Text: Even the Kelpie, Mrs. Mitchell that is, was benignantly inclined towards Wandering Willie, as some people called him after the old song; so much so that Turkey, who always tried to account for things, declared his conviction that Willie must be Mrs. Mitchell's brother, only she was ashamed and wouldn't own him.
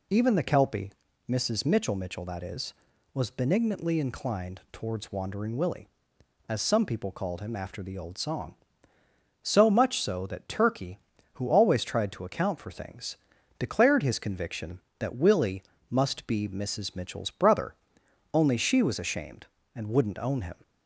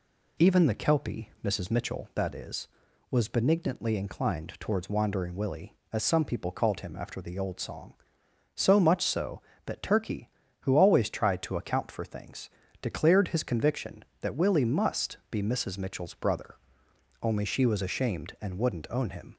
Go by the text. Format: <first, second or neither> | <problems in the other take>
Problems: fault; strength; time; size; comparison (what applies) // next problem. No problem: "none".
second | says "Mitchell" twice; at 1.9 s // pauses between "Willie" and "must"; slight; at 15.6 s; 0.26 s long